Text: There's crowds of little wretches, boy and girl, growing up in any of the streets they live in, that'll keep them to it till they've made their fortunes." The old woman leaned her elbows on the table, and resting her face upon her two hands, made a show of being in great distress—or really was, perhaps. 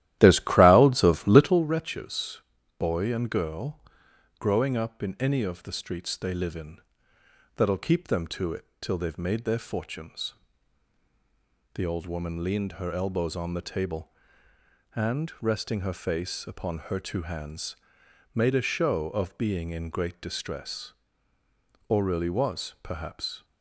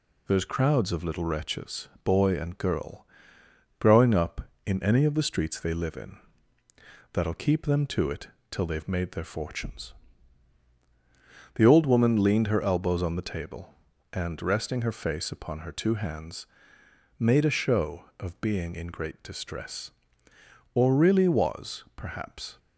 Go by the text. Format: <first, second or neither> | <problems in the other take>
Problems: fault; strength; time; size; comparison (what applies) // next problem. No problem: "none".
second | starts louder than the rest; strong; until 1.7 s; 13.5 dB // pauses between "it" and "till"; slight; at 8.6 s; 0.16 s long; slight in the second